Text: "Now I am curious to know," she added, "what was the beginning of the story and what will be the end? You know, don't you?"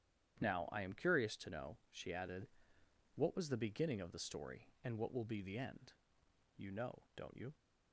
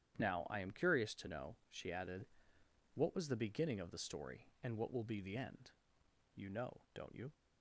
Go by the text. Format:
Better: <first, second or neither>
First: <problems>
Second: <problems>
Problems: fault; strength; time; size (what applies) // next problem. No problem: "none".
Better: neither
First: starts louder than the rest; strong; until 1.4 s; 9.5 dB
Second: starts louder than the rest; strong; until 1.2 s; 9.5 dB